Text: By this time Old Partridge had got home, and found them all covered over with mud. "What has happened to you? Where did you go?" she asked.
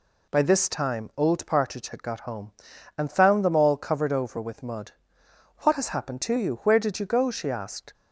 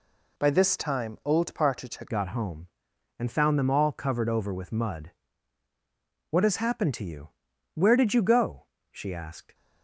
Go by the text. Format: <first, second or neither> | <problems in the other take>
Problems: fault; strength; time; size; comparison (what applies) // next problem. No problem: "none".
first | changes voice at "got"; from 2.0 s on; 7.5 s long